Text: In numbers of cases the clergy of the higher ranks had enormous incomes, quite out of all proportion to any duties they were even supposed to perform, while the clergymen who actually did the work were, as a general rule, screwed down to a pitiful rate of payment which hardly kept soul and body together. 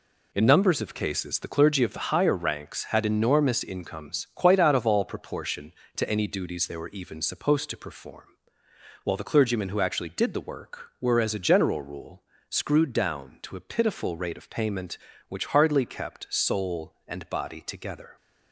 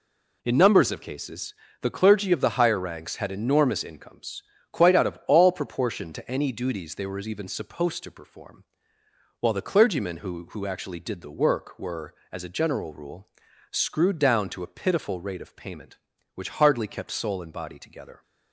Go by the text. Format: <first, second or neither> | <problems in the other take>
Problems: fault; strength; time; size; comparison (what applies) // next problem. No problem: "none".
first | pauses between "cases" and "the"; slight; at 1.5 s; 0.28 s long // says "who" twice; at 10.5 s